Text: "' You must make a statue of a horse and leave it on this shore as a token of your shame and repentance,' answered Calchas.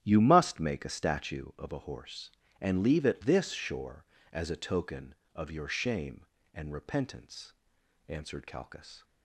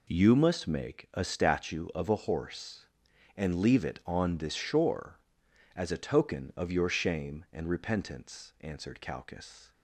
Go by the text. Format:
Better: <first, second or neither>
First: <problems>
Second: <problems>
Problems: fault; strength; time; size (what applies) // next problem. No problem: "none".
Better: second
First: starts louder than the rest; strong; until 1.0 s; 11.5 dB // skips "on"; at 3.2 s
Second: none